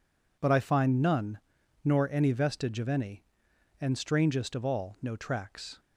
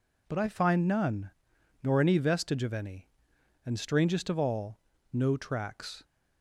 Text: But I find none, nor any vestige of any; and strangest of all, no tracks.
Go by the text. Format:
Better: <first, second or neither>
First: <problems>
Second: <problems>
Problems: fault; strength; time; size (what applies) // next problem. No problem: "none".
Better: neither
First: none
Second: none